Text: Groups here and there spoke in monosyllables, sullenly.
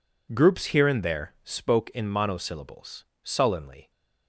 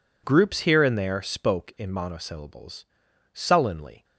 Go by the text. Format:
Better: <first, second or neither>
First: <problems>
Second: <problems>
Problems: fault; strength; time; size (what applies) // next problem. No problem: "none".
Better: neither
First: none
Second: none